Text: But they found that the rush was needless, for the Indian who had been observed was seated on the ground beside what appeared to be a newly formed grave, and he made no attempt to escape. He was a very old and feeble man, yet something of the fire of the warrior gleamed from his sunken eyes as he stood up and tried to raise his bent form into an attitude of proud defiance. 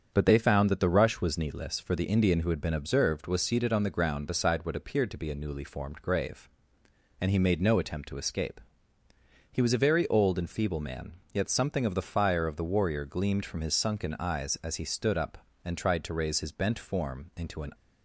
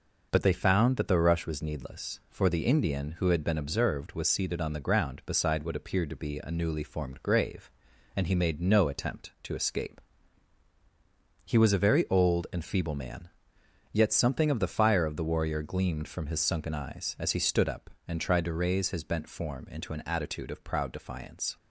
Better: second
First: starts louder than the rest; strong; until 1.1 s; 7.5 dB // stops before "attitude of proud defiance"; at 17.7 s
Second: none

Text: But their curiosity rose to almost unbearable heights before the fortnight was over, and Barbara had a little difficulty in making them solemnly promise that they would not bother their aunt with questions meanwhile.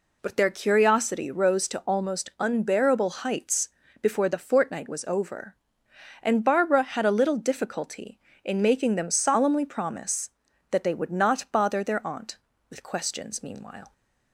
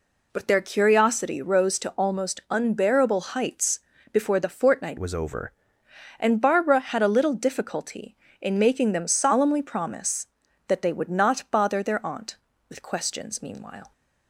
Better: first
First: pauses between "heights" and "before"; slight; at 3.6 s; 0.32 s long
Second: pauses between "heights" and "before"; slight; at 3.7 s; 0.32 s long // changes voice from "was" to "over"; from 4.9 to 5.5 s; 0.6 s long

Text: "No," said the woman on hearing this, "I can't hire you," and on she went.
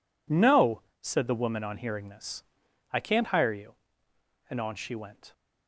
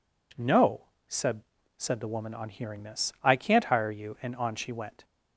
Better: first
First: none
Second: says "said" twice; at 1.7 s

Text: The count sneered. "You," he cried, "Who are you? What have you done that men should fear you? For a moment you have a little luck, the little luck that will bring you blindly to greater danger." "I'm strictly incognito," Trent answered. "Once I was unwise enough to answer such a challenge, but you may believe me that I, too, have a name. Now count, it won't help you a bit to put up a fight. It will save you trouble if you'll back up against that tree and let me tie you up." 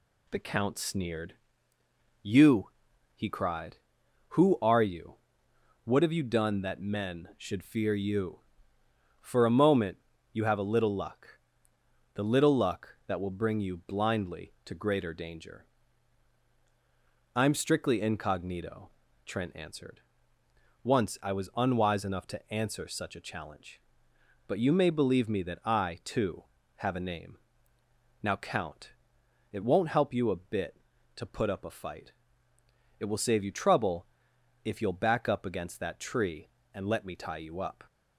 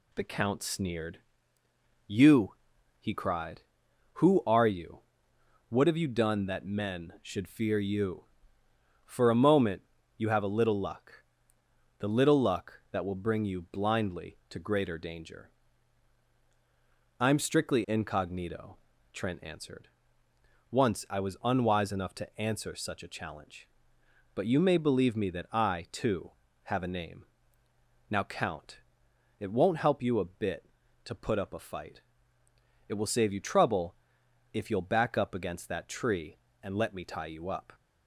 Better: neither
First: pauses between "moment" and "you"; slight; at 9.9 s; 0.34 s long // pauses between "trouble" and "if"; noticeable; at 34.0 s; 0.58 s long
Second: pauses between "moment" and "you"; slight; at 9.8 s; 0.34 s long // pauses between "trouble" and "if"; noticeable; at 33.9 s; 0.58 s long

